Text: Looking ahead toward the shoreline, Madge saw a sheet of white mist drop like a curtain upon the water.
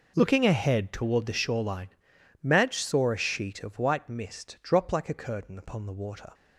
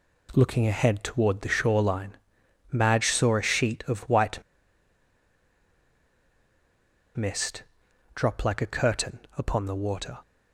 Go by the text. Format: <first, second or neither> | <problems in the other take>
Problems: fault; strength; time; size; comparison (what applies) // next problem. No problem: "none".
first | pauses between "white" and "mist"; strong; at 4.3 s; 2.7 s long // pauses between "mist" and "drop"; noticeable; at 7.6 s; 0.52 s long // pauses between "curtain" and "upon"; slight; at 9.1 s; 0.18 s long